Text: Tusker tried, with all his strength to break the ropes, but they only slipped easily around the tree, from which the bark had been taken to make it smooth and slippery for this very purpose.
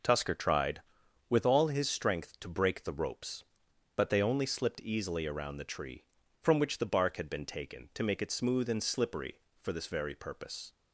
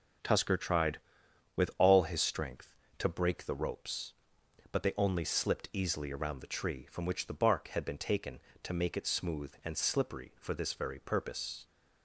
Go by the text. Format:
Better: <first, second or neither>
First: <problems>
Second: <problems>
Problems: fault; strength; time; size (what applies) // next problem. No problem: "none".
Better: neither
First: none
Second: none